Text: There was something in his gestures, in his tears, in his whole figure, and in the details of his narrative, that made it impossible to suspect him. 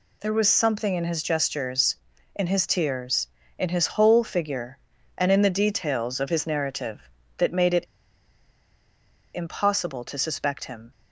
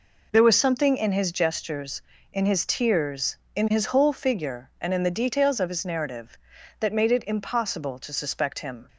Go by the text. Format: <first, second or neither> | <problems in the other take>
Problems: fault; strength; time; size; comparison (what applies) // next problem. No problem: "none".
second | pauses between "it" and "impossible"; strong; at 7.8 s; 1.5 s long